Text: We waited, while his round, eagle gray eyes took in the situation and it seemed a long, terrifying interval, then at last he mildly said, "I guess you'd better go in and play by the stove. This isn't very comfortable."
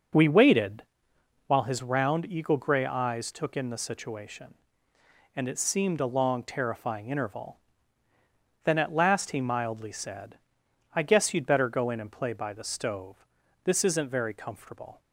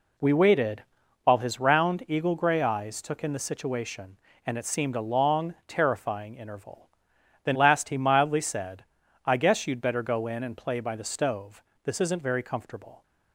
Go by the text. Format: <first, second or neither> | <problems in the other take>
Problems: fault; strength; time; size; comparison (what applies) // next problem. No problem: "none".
first | skips "at"; at 7.5 s